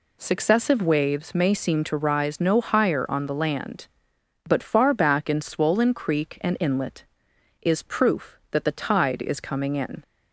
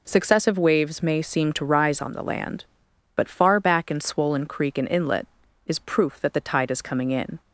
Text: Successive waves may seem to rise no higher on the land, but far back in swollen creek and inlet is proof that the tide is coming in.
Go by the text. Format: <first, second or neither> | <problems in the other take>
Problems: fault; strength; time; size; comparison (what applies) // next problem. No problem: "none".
first | skips "no higher"; at 2.0 s